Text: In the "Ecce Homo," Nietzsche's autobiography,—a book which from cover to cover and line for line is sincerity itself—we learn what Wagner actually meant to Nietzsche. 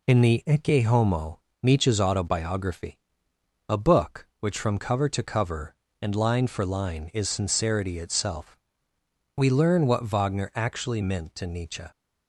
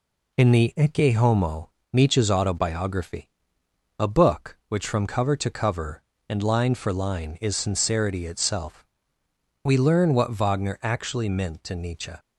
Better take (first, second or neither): neither